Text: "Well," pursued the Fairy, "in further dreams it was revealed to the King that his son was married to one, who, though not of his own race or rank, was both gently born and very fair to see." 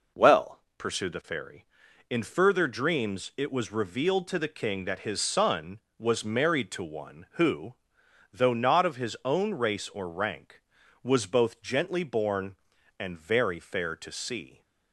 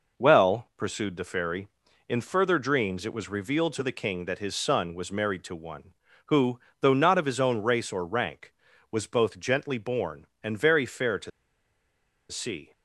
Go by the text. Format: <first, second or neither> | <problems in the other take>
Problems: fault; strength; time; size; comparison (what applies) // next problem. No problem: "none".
first | pauses between "to" and "see"; at 11.3 s; 1.0 s long